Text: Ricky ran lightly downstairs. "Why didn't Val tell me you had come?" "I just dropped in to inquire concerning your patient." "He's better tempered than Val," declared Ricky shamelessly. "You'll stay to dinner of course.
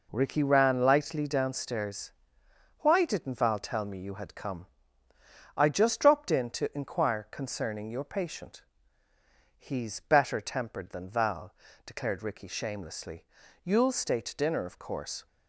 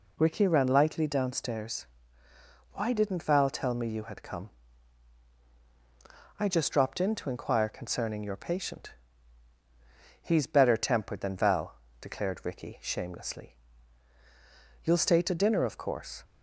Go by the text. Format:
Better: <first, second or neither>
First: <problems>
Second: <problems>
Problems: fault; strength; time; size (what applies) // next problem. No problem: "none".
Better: neither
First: none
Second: none